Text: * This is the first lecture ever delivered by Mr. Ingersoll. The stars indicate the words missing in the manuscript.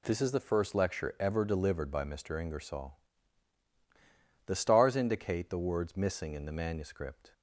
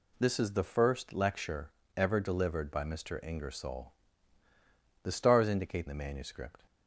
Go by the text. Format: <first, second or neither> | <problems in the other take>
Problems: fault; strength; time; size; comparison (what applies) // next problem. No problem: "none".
first | pauses between "lecture" and "ever"; slight; at 1.7 s; 0.26 s long // skips "the words missing in"; at 5.8 s